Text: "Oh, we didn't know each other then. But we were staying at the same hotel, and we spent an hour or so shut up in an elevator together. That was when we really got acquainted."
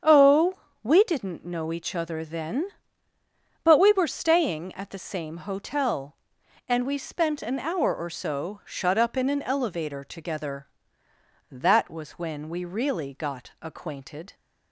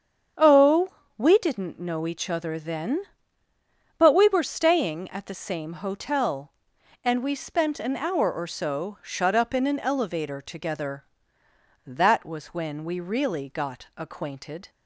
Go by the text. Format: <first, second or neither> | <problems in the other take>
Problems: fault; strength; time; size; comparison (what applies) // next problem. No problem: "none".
neither | starts louder than the rest; strong; the same in both